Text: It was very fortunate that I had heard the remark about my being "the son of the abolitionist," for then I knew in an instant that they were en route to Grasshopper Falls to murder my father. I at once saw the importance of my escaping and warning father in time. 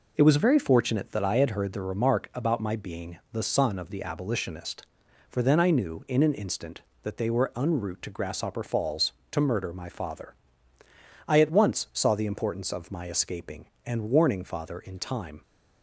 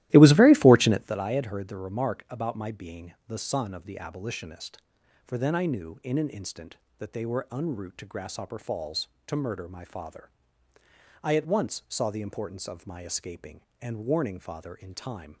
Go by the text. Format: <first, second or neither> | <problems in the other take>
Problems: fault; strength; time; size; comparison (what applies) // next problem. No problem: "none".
first | starts louder than the rest; strong; until 1.2 s; 15.5 dB // pauses between "being" and "the"; slight; at 3.1 s; 0.16 s long; slight in the first